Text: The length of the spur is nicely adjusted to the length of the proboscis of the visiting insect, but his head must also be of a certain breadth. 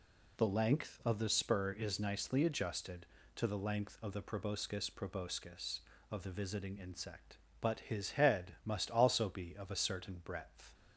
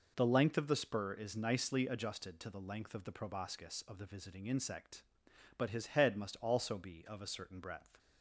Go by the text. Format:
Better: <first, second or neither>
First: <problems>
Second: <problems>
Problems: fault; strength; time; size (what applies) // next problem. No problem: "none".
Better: second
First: says "proboscis" twice; at 4.8 s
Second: none